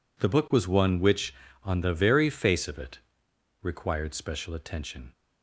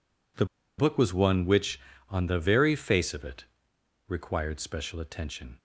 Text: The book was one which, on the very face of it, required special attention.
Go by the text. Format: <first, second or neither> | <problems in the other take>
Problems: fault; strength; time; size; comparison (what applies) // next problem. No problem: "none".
first | pauses between "The" and "book"; slight; at 0.4 s; 0.33 s long